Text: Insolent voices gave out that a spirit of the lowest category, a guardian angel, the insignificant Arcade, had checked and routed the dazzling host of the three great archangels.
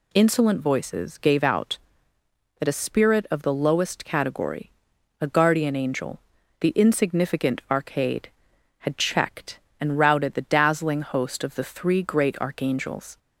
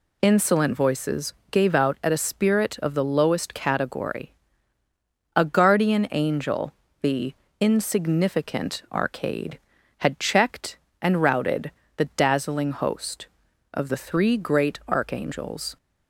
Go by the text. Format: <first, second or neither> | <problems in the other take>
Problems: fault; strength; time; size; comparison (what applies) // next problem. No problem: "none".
first | pauses between "voices" and "gave"; slight; at 1.3 s; 0.18 s long // says "at" for "that"; at 2.0 s // pauses between "the" and "insignificant"; slight; at 7.3 s; 0.24 s long // pauses between "routed" and "the"; slight; at 11.7 s; 0.26 s long